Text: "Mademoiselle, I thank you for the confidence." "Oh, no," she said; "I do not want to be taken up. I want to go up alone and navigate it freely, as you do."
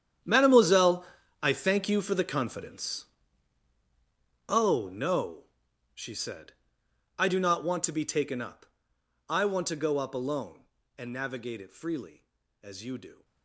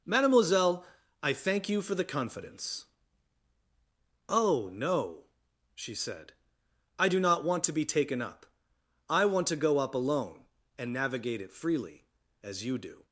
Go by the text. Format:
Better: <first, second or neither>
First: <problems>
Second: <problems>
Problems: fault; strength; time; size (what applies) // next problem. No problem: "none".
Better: second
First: gets quieter; strong; throughout; 15.5 dB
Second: none